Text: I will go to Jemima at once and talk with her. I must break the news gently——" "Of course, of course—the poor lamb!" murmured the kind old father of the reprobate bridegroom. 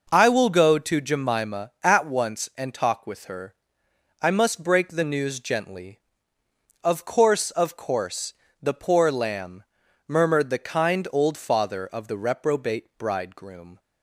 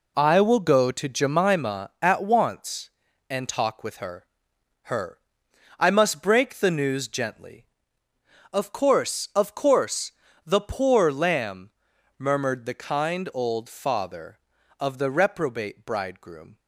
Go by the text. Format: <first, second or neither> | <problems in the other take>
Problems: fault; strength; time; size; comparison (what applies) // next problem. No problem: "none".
first | says "her" twice; at 4.8 s